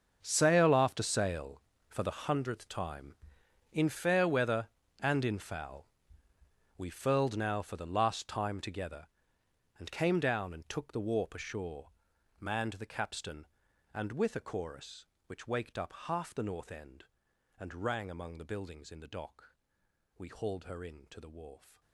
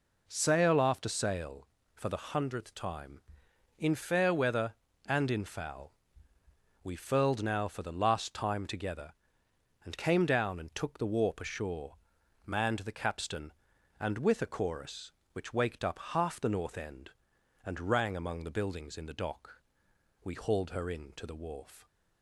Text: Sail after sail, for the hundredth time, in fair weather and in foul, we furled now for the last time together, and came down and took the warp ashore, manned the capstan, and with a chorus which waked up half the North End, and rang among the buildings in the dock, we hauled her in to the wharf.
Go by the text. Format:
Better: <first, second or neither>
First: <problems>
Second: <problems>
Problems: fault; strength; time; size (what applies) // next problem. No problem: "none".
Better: second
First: gets quieter; strong; throughout; 15.5 dB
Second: none